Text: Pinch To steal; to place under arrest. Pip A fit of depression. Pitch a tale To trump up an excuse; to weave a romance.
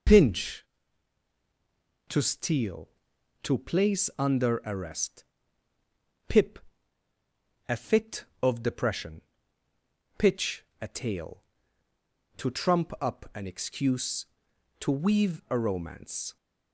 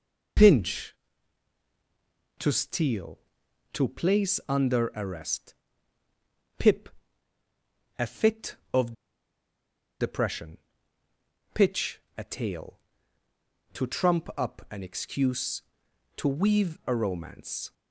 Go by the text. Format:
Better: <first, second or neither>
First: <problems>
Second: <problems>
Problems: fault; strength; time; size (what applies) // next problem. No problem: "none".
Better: first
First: pauses between "Pip" and "A"; at 6.5 s; 1.0 s long // pauses between "Pitch" and "a"; slight; at 10.6 s; 0.18 s long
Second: pauses between "Pip" and "A"; at 6.8 s; 1.0 s long // pauses between "of" and "depression"; at 8.9 s; 1.0 s long // pauses between "Pitch" and "a"; slight; at 11.9 s; 0.18 s long